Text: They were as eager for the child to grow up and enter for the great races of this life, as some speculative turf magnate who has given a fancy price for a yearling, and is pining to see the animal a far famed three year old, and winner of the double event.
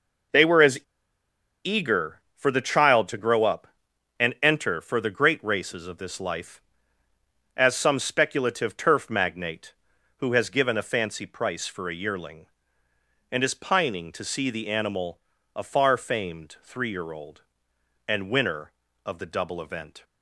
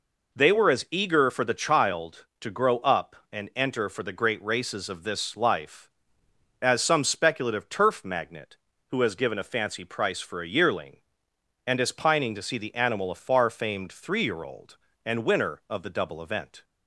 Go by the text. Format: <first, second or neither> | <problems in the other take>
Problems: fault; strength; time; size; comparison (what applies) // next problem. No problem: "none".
second | pauses between "as" and "eager"; noticeable; at 0.7 s; 0.86 s long // pauses between "animal" and "a"; slight; at 15.1 s; 0.36 s long